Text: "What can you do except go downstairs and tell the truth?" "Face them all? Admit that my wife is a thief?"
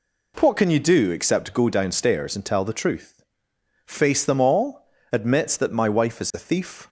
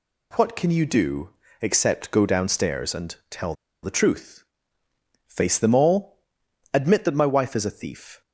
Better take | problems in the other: first | pauses between "do" and "except"; slight; at 1.2 s; 0.32 s long // pauses between "tell" and "the"; slight; at 3.5 s; 0.29 s long

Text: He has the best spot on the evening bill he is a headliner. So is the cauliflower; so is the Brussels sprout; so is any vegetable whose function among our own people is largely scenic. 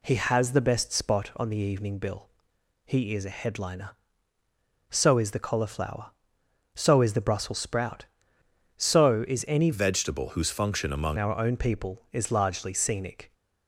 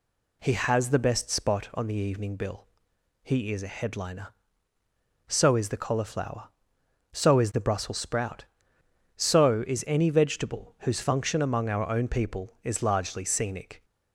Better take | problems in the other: second | pauses between "bill" and "he"; noticeable; at 2.2 s; 0.58 s long; noticeable in the second // changes voice from "vegetable" to "among"; from 9.7 to 11.1 s; 1.4 s long

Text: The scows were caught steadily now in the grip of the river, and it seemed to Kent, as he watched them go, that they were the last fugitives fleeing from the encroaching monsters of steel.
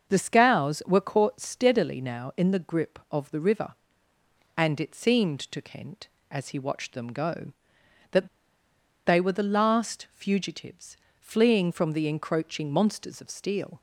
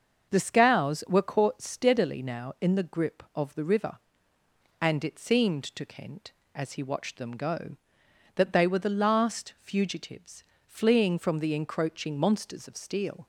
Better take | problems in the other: second | starts louder than the rest; until 1.1 s; 6.5 dB; also in the second // pauses between "that" and "they"; noticeable; at 8.2 s; 0.77 s long // pauses between "fugitives" and "fleeing"; slight; at 10.9 s; 0.24 s long; slight in the second

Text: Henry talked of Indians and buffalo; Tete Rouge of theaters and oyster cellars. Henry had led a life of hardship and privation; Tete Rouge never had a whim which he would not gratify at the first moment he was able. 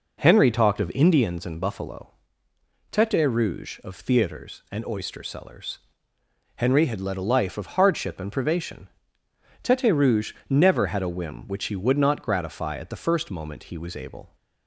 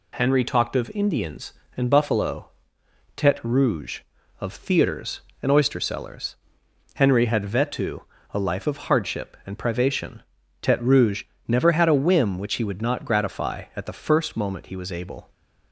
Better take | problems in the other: first | says "vetu" for "led"; at 7.4 s // pauses between "Rouge" and "never"; slight; at 11.2 s; 0.24 s long; slight in the first

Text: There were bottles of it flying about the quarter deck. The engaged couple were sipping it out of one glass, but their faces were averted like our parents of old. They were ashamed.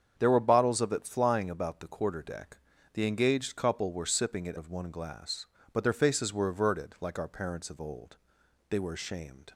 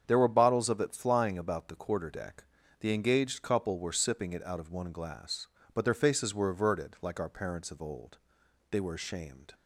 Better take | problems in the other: second | starts louder than the rest; strong; until 1.1 s; 7.5 dB; strong in the second // skips "out"; at 4.5 s

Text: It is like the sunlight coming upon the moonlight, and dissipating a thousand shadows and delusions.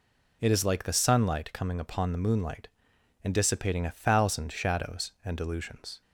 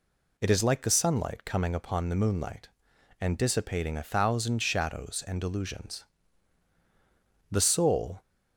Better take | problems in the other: first | goes on to say "The soul"; noticeable; from 7.5 s on; 0.70 s long

